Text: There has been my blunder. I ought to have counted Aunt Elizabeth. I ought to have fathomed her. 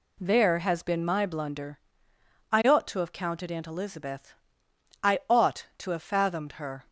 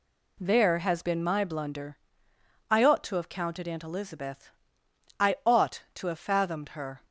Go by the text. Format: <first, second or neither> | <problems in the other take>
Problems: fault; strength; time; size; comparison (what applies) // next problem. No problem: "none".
neither | none